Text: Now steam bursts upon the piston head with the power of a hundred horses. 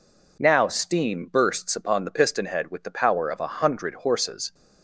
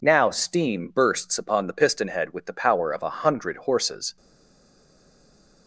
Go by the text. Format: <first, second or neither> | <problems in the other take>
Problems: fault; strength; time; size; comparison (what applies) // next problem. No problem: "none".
first | stays silent after the last word; noticeable; from 4.1 s on; 1.5 s long